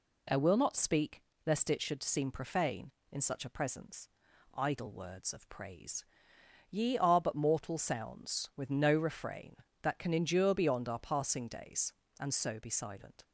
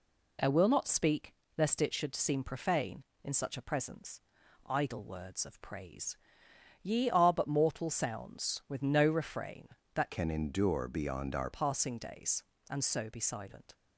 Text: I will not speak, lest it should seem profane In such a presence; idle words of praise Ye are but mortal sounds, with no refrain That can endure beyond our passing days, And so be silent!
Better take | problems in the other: first | pauses between "praise" and "Ye"; noticeable; at 6.1 s; 0.66 s long; noticeable in the first // changes voice from "can" to "our"; from 10.1 to 11.5 s; 1.4 s long

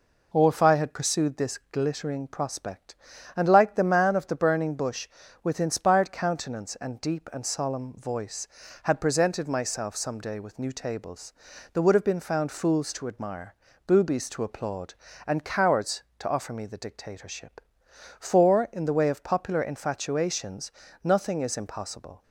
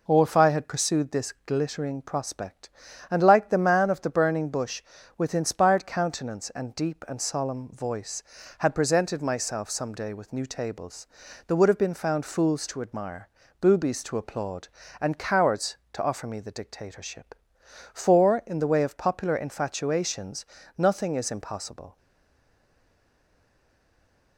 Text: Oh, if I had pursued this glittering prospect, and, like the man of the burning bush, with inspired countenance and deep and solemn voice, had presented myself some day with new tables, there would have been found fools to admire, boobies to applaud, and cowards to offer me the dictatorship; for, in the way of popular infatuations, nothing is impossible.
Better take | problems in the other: first | stays silent after the last word; from 21.9 s on; 2.4 s long

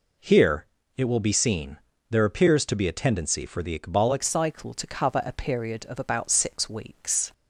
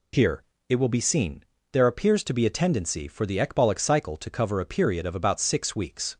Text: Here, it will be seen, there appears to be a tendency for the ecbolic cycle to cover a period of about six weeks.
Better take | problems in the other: second | changes voice at "cycle"; from 4.2 s on; 3.1 s long

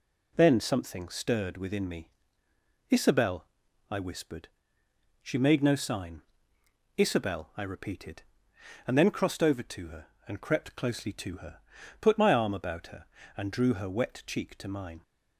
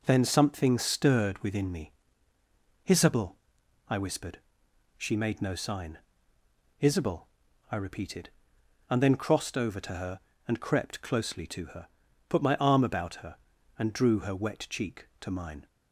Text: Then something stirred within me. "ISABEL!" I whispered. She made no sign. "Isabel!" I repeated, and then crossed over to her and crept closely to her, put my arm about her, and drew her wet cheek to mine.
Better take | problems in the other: neither | none

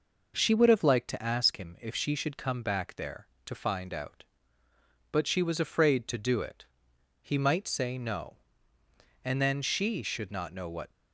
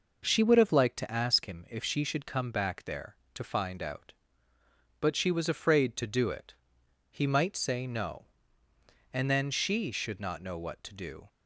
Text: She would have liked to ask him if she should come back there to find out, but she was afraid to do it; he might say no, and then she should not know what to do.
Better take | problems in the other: second | stops before "to do"; at 10.9 s

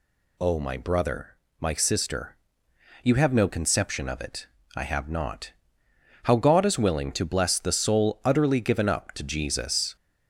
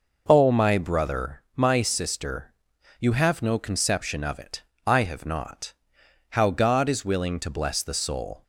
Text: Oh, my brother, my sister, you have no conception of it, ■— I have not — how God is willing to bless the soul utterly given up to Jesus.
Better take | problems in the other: first | stops before "utterly given up to Jesus"; at 8.4 s

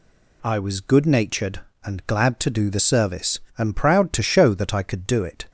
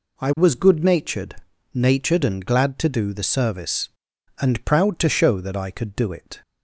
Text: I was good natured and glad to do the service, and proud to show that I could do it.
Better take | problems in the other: first | says "natured" twice; at 1.7 s

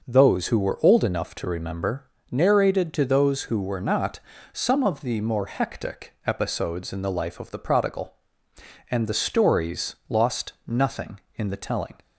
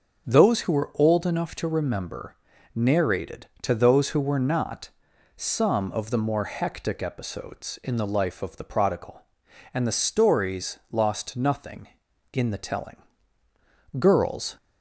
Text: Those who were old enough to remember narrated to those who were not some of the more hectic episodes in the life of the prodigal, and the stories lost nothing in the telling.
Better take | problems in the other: first | starts louder than the rest; until 1.3 s; 6.5 dB // pauses between "remember" and "narrated"; at 2.3 s; 0.40 s long; slight in the first // pauses between "not" and "some"; noticeable; at 4.8 s; 0.48 s long; slight in the first // goes on to say "Girls"; from 13.9 s on; 0.58 s long

